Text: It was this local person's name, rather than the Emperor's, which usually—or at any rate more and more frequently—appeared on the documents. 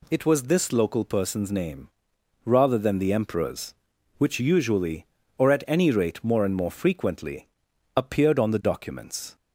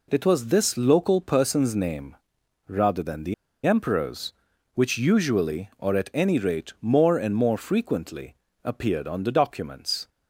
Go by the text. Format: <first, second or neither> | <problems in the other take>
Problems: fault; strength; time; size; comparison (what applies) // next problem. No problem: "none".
first | pauses between "the" and "Emperor's"; slight; at 3.3 s; 0.32 s long